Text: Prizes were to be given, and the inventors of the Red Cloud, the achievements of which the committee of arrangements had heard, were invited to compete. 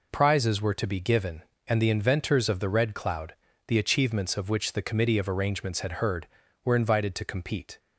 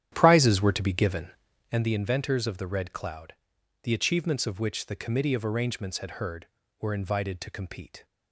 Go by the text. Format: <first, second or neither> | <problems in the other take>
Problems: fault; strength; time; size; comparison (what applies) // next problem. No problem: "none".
first | starts louder than the rest; strong; until 1.9 s; 10.5 dB